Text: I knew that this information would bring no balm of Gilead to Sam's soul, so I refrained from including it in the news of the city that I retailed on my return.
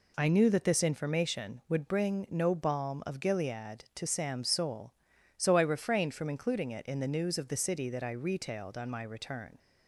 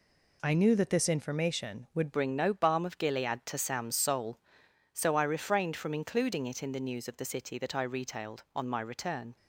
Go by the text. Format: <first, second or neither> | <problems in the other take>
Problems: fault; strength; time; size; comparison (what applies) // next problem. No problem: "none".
first | changes voice at "bring"; from 2.1 s on; 7.2 s long